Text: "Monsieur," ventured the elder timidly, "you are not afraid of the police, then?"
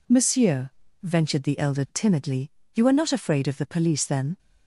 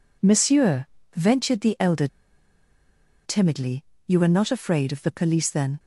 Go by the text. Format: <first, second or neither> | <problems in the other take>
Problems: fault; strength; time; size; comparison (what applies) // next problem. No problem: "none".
first | pauses between "elder" and "timidly"; at 2.0 s; 1.1 s long